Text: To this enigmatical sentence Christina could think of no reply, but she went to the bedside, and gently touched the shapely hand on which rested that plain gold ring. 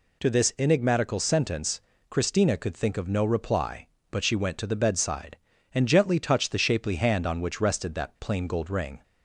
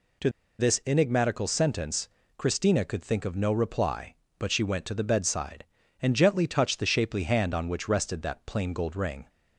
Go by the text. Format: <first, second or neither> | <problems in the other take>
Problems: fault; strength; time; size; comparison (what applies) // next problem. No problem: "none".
first | pauses between "To" and "this"; slight; at 0.2 s; 0.29 s long // pauses between "sentence" and "Christina"; slight; at 2.0 s; 0.28 s long; slight in the first